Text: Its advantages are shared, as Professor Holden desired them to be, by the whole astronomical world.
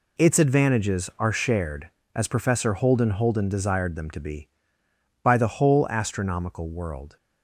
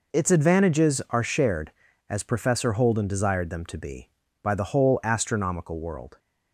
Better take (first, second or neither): second